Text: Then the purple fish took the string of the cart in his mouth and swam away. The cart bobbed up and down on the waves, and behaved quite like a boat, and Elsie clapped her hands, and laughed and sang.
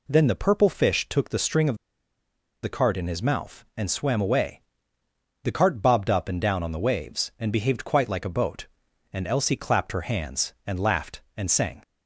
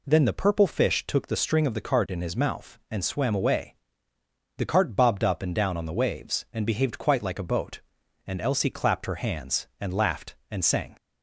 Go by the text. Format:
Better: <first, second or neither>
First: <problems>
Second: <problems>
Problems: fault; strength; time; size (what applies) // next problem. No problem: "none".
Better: second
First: pauses between "of" and "the"; noticeable; at 1.7 s; 0.86 s long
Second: none